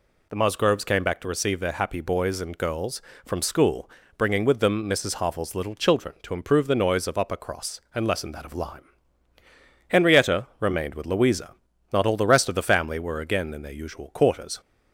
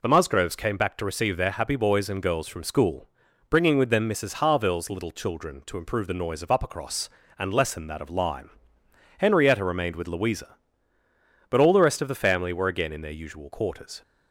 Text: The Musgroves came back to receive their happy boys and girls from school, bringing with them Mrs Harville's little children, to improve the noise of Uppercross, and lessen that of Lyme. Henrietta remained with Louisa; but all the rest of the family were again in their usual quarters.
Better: second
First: says "not" for "but"; at 11.9 s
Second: none

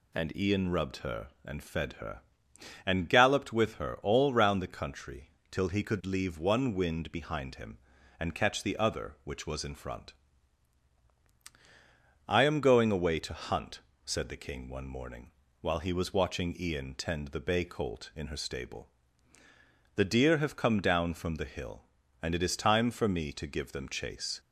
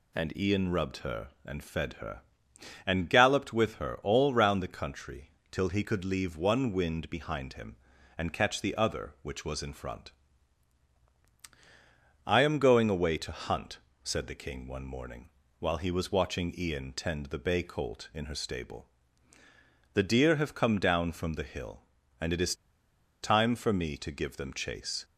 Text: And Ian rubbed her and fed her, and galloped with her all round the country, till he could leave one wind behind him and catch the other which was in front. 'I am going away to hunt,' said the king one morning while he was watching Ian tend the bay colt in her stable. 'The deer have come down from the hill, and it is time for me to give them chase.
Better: first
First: pauses between "morning" and "while"; slight; at 15.3 s; 0.28 s long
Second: pauses between "morning" and "while"; slight; at 15.2 s; 0.28 s long // pauses between "is" and "time"; noticeable; at 22.5 s; 0.68 s long

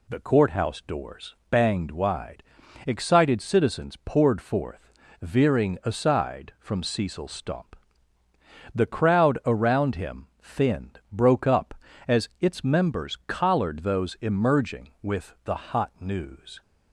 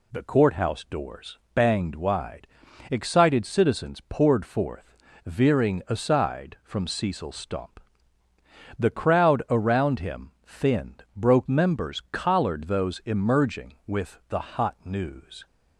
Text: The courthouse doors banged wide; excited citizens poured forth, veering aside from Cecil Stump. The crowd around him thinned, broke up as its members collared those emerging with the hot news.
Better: first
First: none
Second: pauses between "doors" and "banged"; slight; at 1.3 s; 0.16 s long // skips "up as its"; at 11.4 s

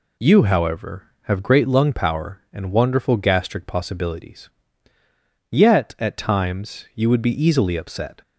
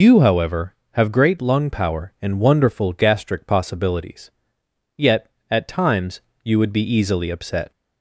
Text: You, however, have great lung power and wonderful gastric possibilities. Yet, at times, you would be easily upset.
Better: first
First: none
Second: loses the start of "You"; at 0.0 s; 75 ms

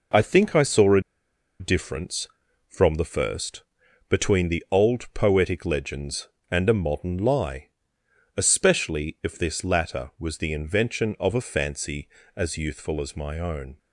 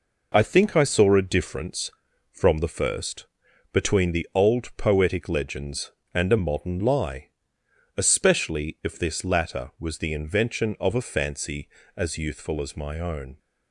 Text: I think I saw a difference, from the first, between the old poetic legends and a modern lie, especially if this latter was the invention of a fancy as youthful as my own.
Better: second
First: pauses between "a" and "difference"; noticeable; at 1.0 s; 0.59 s long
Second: none

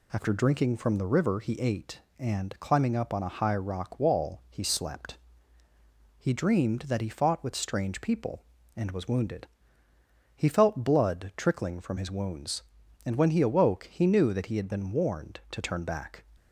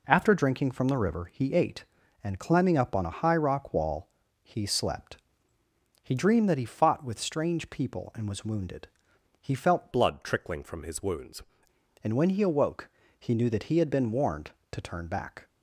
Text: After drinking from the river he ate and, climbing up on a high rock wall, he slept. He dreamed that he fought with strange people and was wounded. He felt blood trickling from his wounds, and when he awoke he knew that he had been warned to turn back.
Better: first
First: none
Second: changes voice from "blood" to "wounds"; from 9.9 to 11.4 s; 1.5 s long // pauses between "awoke" and "he"; slight; at 12.8 s; 0.32 s long

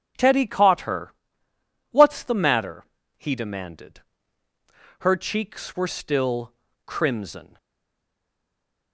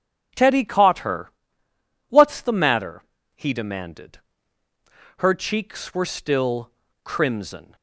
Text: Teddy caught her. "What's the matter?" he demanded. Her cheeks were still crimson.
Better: second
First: pauses between "still" and "crimson"; slight; at 6.5 s; 0.32 s long // stays silent after the last word; noticeable; from 7.5 s on; 1.4 s long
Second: pauses between "still" and "crimson"; slight; at 6.7 s; 0.32 s long

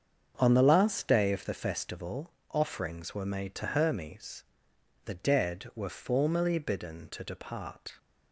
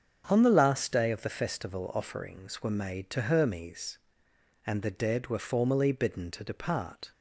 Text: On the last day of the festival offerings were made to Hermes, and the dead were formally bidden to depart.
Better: second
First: starts louder than the rest; strong; until 1.3 s; 7.5 dB // pauses between "festival" and "offerings"; slight; at 2.2 s; 0.22 s long // skips "and"; at 4.7 s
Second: starts louder than the rest; until 1.2 s; 7 dB

